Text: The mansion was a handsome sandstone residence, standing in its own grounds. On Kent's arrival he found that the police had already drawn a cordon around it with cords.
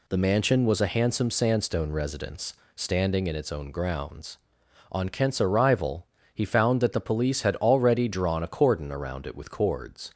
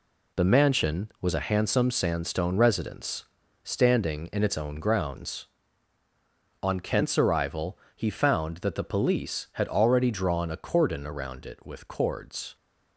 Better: first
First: pauses between "arrival" and "he"; slight; at 6.0 s; 0.28 s long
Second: gets quieter; strong; throughout; 7.5 dB // pauses between "arrival" and "he"; slight; at 7.7 s; 0.18 s long

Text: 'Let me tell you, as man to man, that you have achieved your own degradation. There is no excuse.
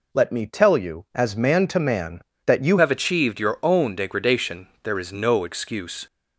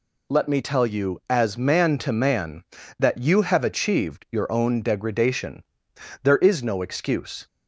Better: second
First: changes voice at "have"; from 2.7 s on; 3.3 s long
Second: none

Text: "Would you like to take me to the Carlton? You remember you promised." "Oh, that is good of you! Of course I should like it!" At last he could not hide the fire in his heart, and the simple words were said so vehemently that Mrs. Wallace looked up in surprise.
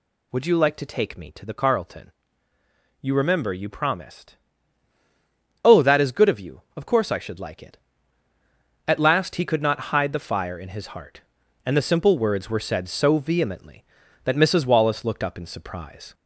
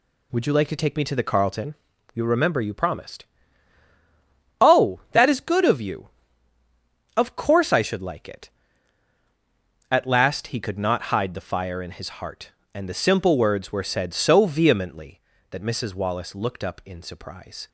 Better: second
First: gets louder; slight; throughout; 2.5 dB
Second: none

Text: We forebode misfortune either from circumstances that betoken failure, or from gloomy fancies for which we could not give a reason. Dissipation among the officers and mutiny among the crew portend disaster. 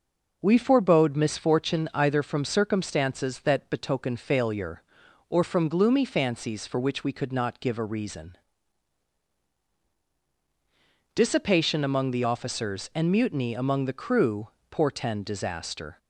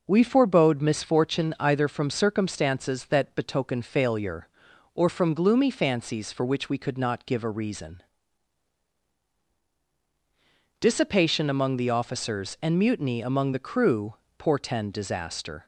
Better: neither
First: pauses between "crew" and "portend"; slight; at 14.4 s; 0.20 s long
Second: pauses between "crew" and "portend"; slight; at 14.1 s; 0.22 s long

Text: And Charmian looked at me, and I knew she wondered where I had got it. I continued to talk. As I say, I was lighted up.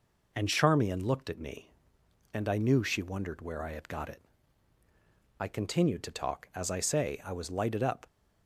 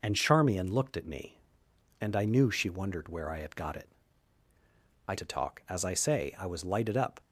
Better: first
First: none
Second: skips "continued"; at 5.1 s

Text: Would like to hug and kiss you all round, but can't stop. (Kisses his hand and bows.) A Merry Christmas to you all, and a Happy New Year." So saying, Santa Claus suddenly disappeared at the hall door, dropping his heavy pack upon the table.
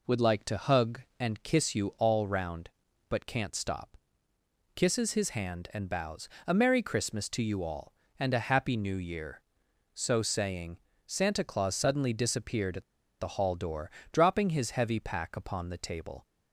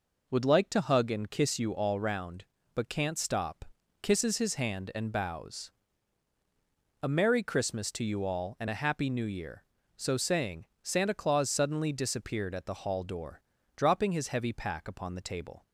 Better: second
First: pauses between "at" and "the"; slight; at 12.8 s; 0.34 s long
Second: none

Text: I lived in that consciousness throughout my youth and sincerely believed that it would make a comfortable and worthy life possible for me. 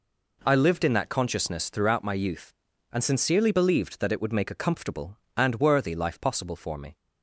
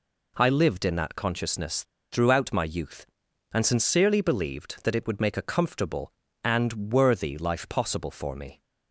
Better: first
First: none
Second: pauses between "consciousness" and "throughout"; slight; at 1.8 s; 0.27 s long

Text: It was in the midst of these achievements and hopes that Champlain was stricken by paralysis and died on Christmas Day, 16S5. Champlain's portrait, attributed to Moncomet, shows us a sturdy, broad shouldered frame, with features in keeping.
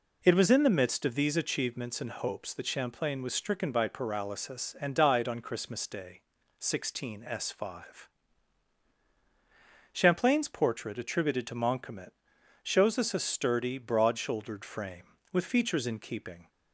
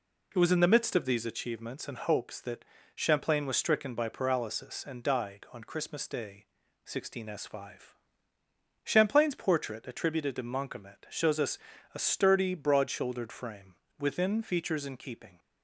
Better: first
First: none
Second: pauses between "that" and "Champlain"; slight; at 2.6 s; 0.30 s long // pauses between "us" and "a"; slight; at 11.5 s; 0.34 s long // says "within" for "with"; at 13.9 s

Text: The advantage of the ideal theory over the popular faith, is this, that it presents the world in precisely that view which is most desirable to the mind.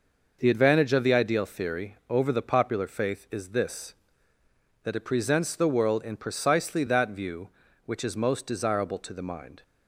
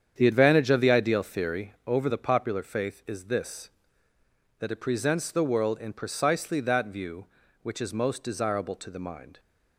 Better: first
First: none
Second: starts louder than the rest; strong; until 1.9 s; 8 dB

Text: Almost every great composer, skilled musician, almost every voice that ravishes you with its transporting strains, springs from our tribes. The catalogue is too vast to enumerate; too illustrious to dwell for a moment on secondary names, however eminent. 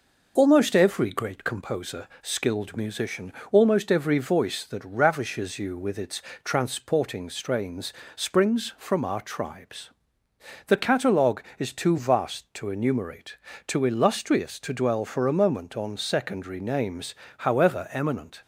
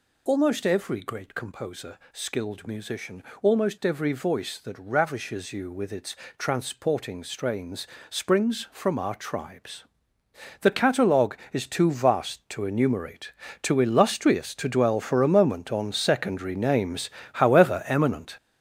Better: first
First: pauses between "its" and "transporting"; slight; at 6.2 s; 0.24 s long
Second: gets louder; strong; throughout; 8 dB // pauses between "its" and "transporting"; slight; at 6.1 s; 0.24 s long

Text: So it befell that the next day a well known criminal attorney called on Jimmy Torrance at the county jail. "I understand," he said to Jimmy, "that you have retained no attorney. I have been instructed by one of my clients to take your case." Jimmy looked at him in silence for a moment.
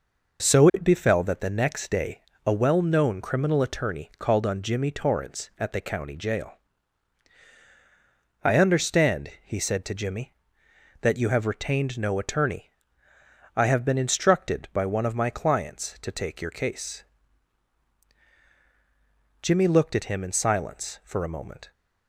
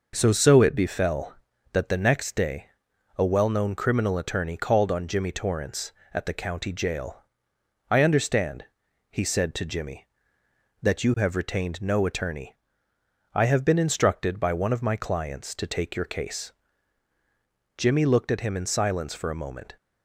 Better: first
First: pauses between "day" and "a"; slight; at 2.2 s; 0.24 s long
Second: says "So" twice; at 0.3 s // pauses between "day" and "a"; noticeable; at 2.6 s; 0.50 s long

